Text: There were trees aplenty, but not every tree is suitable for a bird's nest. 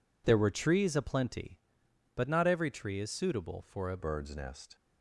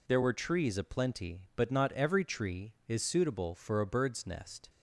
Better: second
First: changes voice at "bird's"; from 3.9 s on; 0.8 s long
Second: none

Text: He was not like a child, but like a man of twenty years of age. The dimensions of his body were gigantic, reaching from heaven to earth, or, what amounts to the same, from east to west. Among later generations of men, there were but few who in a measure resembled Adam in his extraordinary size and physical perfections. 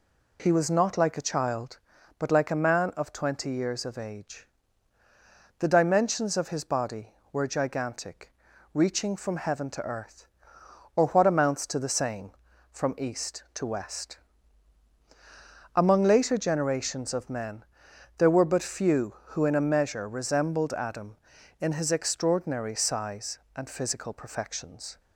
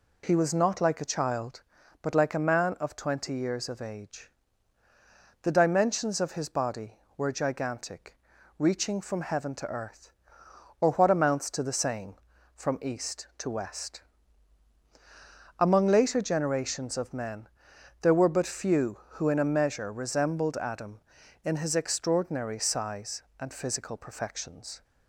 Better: neither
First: none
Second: none

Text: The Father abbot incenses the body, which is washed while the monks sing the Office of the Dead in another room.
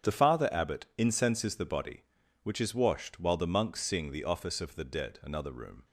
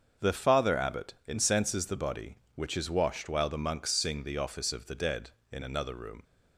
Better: second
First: starts louder than the rest; strong; until 1.2 s; 9 dB // skips "in"; at 5.2 s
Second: starts louder than the rest; until 1.3 s; 6.5 dB

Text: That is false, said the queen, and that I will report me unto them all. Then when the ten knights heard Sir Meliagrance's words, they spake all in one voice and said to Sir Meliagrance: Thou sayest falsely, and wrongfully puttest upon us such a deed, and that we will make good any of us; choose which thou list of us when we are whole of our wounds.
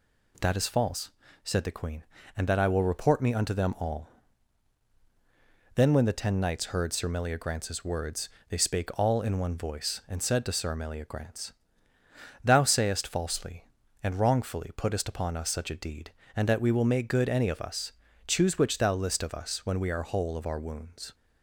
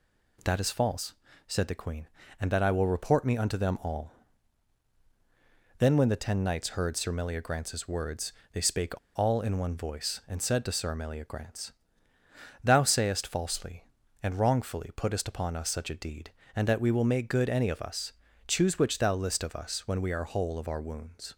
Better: first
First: none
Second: pauses between "spake" and "all"; slight; at 8.9 s; 0.18 s long

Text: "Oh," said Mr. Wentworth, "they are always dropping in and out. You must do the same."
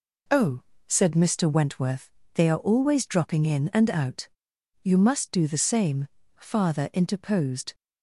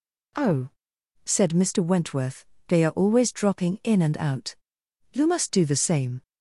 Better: second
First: goes on to say "Father interposed"; from 6.3 s on; 1.3 s long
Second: none

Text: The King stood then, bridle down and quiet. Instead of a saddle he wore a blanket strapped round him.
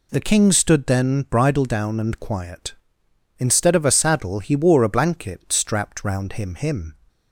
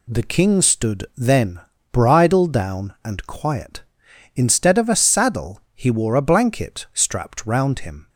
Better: second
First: says "him" twice; at 6.5 s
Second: none

